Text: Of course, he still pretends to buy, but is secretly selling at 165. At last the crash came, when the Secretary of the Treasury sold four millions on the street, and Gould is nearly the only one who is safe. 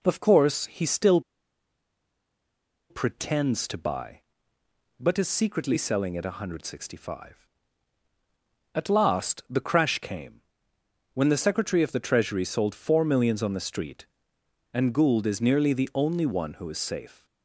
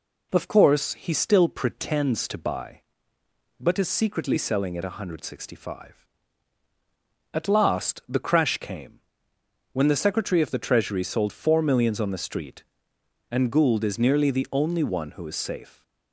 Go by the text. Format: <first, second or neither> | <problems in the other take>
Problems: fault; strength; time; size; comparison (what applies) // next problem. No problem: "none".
second | pauses between "still" and "pretends"; strong; at 1.1 s; 1.7 s long